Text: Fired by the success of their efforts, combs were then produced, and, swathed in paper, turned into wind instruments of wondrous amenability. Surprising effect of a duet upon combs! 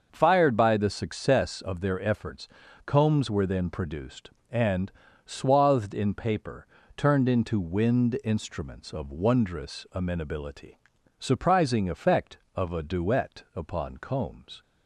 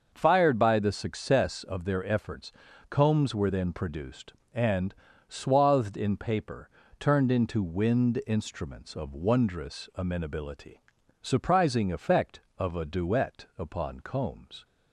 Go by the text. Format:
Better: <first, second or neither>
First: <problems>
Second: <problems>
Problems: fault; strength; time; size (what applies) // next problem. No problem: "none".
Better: neither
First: starts louder than the rest; until 1.1 s; 6.5 dB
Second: starts louder than the rest; until 1.1 s; 6.5 dB